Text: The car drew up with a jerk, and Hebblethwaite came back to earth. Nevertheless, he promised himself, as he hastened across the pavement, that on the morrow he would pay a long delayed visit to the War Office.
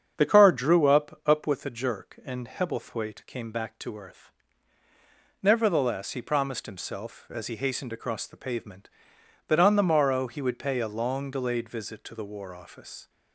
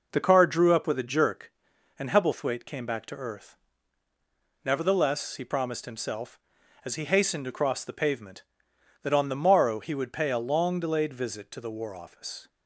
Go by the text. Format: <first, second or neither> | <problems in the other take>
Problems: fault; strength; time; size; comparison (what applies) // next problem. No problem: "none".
second | starts louder than the rest; strong; until 1.1 s; 7.5 dB // says "up" twice; at 1.2 s